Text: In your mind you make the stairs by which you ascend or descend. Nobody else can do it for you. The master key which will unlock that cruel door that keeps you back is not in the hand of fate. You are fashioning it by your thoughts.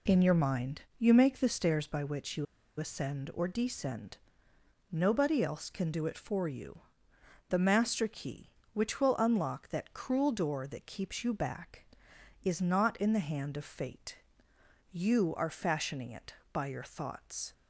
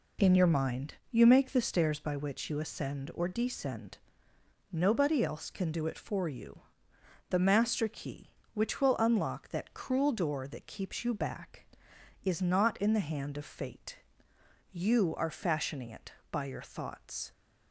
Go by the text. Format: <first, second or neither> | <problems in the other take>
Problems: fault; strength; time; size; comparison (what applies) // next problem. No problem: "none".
second | pauses between "mind" and "you"; slight; at 0.8 s; 0.16 s long; slight in the second // pauses between "you" and "ascend"; slight; at 2.4 s; 0.33 s long